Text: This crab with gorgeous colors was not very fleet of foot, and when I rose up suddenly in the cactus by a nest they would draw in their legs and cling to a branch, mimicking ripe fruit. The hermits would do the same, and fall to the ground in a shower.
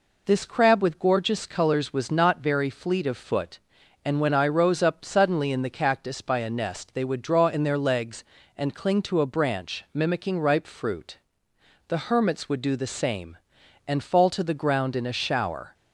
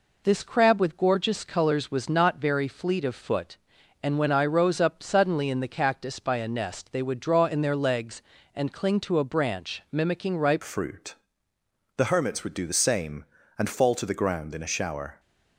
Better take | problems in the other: first | changes voice at "fruit"; from 10.6 s on; 4.5 s long

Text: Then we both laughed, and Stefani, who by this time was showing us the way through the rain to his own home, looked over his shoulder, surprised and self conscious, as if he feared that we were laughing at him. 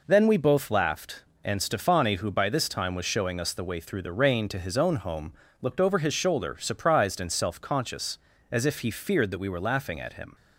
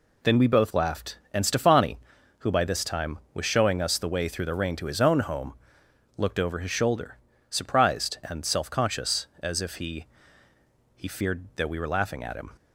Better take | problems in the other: first | says "he" twice; at 10.9 s

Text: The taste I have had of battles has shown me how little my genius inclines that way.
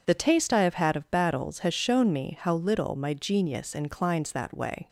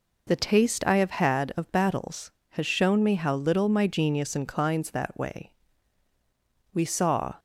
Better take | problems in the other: first | goes on to say "We saw"; noticeable; from 6.7 s on; 0.64 s long

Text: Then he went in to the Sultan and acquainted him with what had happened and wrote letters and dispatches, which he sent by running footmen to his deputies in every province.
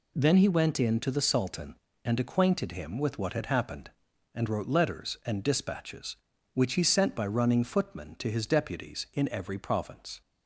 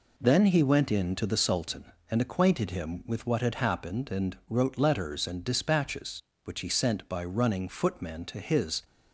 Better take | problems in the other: first | stops before "deputies in every province"; at 8.8 s

